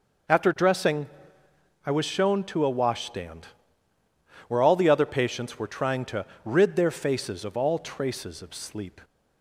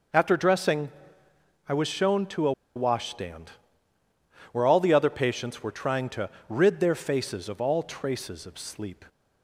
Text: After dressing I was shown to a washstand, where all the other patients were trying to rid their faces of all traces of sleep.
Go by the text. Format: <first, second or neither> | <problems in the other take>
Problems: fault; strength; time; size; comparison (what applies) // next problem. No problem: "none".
first | pauses between "dressing" and "I"; noticeable; at 0.8 s; 0.78 s long; noticeable in the first // pauses between "a" and "washstand"; slight; at 2.5 s; 0.24 s long // pauses between "to" and "rid"; slight; at 6.2 s; 0.18 s long; slight in the first